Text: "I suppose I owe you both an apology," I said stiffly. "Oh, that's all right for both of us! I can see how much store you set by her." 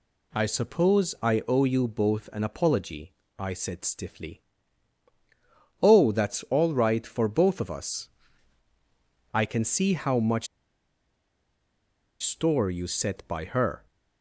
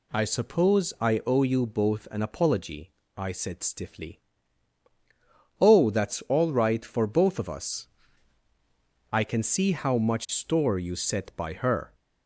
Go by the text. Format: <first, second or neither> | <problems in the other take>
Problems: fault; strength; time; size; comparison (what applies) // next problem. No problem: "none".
second | pauses between "much" and "store"; strong; at 10.4 s; 1.7 s long